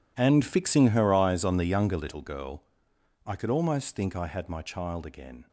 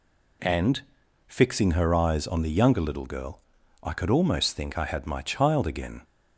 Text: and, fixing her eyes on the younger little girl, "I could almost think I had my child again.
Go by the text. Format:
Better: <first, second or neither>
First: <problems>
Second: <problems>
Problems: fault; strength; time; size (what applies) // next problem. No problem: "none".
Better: second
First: gets quieter; strong; throughout; 17 dB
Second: none